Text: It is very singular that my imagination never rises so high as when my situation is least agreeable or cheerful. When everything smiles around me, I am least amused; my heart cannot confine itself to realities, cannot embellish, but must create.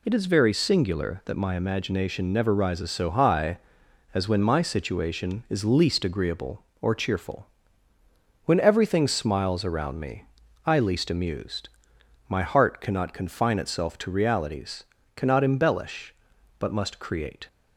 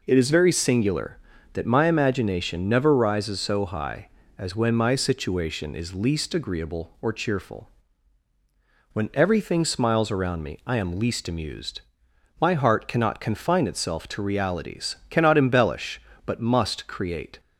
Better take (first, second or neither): second